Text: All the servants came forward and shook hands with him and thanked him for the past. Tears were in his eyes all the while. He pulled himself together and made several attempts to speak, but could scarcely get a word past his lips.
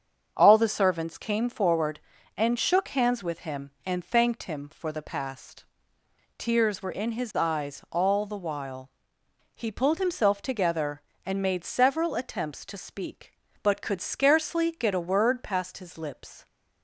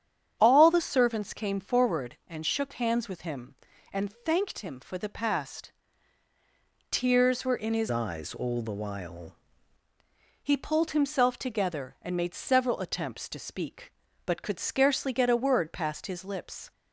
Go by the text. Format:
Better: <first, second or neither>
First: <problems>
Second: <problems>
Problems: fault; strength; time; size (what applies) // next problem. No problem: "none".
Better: first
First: starts louder than the rest; until 1.3 s; 7 dB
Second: starts louder than the rest; strong; until 1.4 s; 9.5 dB // changes voice from "eyes" to "while"; from 7.9 to 9.3 s; 1.4 s long